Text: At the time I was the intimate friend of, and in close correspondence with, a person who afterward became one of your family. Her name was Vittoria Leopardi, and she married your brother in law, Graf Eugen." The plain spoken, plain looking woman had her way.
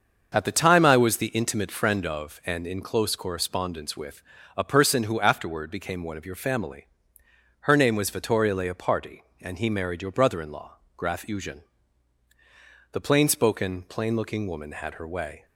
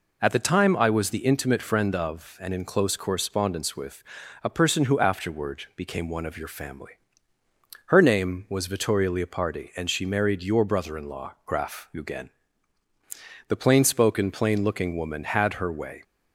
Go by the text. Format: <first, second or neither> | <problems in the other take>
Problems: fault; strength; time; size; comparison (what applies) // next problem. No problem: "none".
second | starts louder than the rest; until 1.3 s; 6.5 dB // says "he" for "she"; at 9.5 s